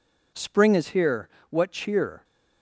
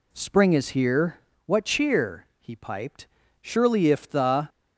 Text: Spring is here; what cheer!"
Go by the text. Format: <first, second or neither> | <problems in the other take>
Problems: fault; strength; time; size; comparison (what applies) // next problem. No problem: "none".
first | goes on to say "he piped Surely if the"; strong; from 2.4 s on; 2.0 s long